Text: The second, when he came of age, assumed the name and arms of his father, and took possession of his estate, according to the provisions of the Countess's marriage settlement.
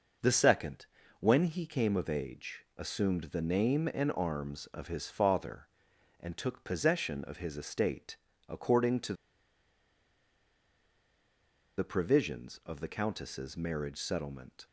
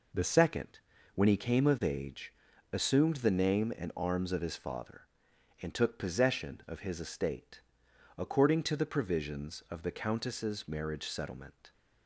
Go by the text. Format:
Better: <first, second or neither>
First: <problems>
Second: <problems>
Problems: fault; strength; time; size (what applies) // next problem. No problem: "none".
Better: second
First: pauses between "to" and "the"; strong; at 9.1 s; 2.6 s long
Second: none